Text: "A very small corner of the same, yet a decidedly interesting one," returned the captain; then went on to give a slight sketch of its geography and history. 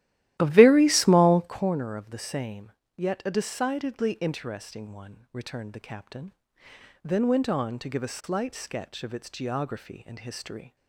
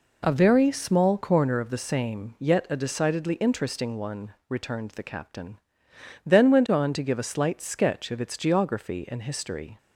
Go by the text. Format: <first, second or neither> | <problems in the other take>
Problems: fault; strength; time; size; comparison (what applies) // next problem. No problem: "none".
second | starts louder than the rest; strong; until 1.7 s; 14.5 dB